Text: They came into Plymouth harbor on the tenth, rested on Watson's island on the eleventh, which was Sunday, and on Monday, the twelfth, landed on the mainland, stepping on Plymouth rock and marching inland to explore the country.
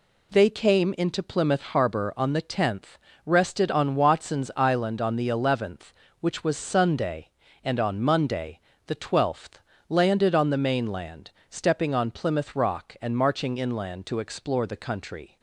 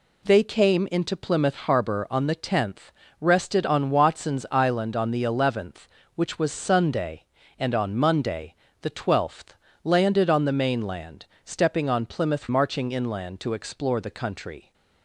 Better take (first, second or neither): first